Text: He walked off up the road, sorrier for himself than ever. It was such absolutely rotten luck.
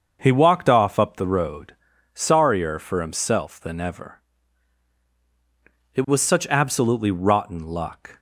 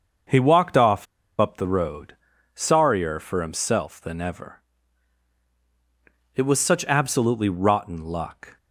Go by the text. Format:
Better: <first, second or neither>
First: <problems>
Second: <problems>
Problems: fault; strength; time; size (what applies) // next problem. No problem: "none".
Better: first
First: starts louder than the rest; until 1.2 s; 6.5 dB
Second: starts louder than the rest; until 1.6 s; 6.5 dB // pauses between "off" and "up"; slight; at 1.0 s; 0.33 s long